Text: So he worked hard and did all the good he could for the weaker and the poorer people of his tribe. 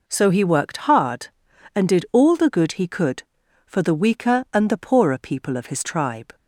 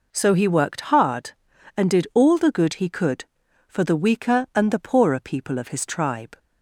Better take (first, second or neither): neither